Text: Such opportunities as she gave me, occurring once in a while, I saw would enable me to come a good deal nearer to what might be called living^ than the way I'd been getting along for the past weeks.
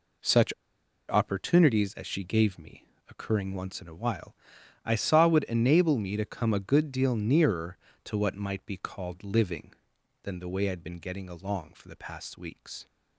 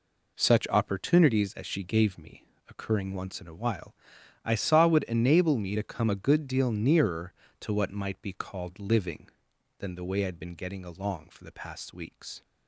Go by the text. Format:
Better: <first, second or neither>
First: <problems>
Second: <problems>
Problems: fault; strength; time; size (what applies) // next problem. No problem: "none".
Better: second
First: pauses between "Such" and "opportunities"; noticeable; at 0.5 s; 0.55 s long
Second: none